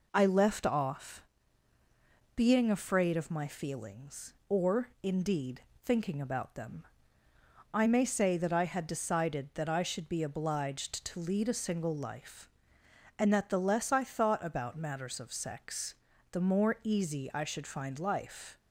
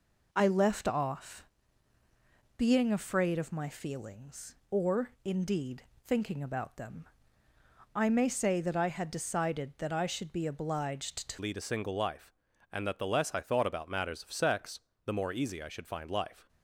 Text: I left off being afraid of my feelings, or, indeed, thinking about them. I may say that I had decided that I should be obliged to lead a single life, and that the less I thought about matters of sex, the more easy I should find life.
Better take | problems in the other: first | pauses between "off" and "being"; at 1.4 s; 1.1 s long; also in the first // changes voice at "lead"; from 11.3 s on; 5.1 s long

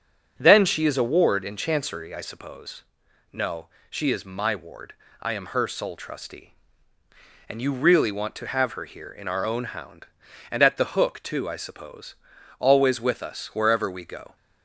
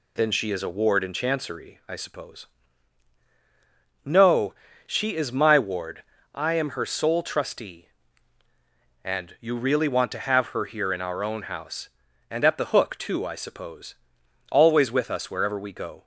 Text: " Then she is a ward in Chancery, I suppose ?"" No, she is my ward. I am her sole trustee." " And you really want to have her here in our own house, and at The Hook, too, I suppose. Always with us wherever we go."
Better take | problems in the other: second | starts louder than the rest; strong; until 1.3 s; 8.5 dB // says "hound" for "house"; at 9.6 s

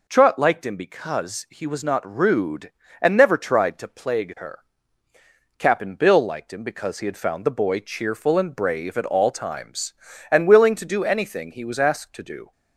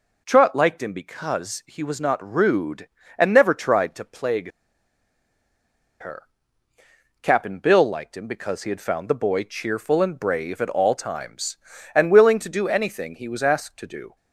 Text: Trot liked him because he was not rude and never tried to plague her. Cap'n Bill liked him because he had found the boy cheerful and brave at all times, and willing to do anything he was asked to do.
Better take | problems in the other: first | pauses between "plague" and "her"; strong; at 4.5 s; 1.5 s long

